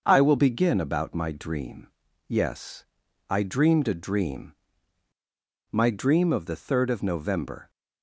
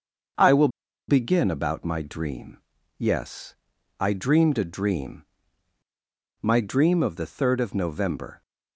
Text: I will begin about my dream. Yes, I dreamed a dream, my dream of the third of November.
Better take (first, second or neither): first